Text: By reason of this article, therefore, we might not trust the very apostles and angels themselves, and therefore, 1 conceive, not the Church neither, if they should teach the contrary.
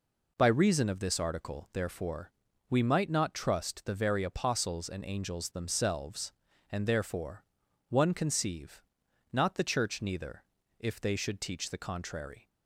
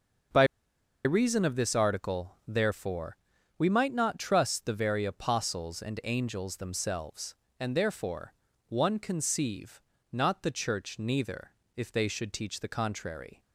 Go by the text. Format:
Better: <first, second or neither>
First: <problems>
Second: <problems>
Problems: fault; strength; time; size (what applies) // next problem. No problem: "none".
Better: first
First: none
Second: starts louder than the rest; until 1.9 s; 6.5 dB // pauses between "By" and "reason"; noticeable; at 0.4 s; 0.60 s long